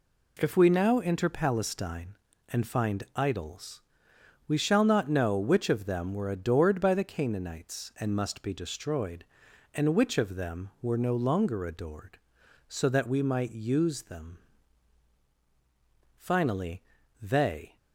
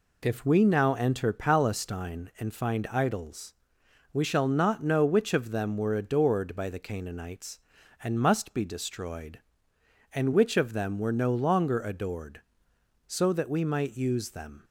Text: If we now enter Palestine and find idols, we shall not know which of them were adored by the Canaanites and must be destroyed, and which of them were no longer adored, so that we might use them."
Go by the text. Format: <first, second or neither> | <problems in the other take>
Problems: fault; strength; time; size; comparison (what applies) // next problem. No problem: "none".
second | goes on to say "Finally they"; from 16.1 s on; 1.5 s long